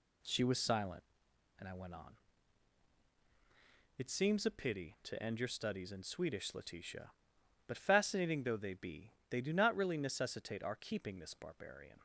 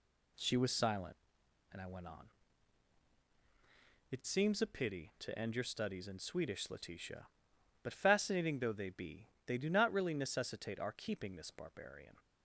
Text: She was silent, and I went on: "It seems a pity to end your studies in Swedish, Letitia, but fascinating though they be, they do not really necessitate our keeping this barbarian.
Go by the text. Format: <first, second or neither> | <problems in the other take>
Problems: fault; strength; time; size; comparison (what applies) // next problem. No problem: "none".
neither | none